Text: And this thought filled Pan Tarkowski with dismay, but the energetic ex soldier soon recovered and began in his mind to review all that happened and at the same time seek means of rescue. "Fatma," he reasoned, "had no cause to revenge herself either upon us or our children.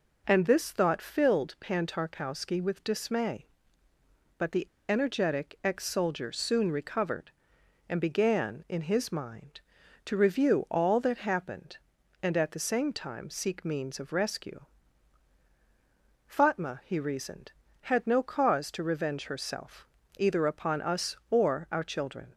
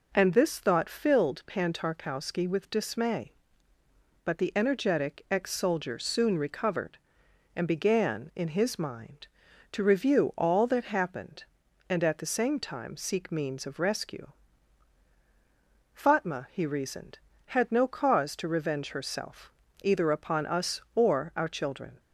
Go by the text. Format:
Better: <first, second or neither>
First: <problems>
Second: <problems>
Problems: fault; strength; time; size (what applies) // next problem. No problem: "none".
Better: second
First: pauses between "the" and "energetic"; slight; at 4.6 s; 0.25 s long // pauses between "herself" and "either"; slight; at 19.8 s; 0.32 s long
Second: pauses between "herself" and "either"; slight; at 19.5 s; 0.32 s long